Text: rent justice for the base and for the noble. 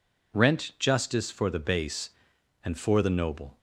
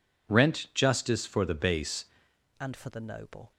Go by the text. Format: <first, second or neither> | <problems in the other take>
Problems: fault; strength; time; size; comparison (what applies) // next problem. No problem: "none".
first | changes voice at "and"; from 2.5 s on; 1.0 s long